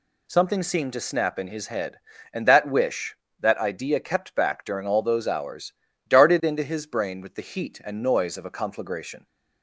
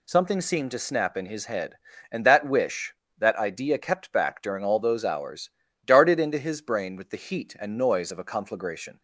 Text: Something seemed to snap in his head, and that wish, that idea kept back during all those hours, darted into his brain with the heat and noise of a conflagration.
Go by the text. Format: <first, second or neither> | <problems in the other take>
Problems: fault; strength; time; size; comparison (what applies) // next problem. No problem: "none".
neither | none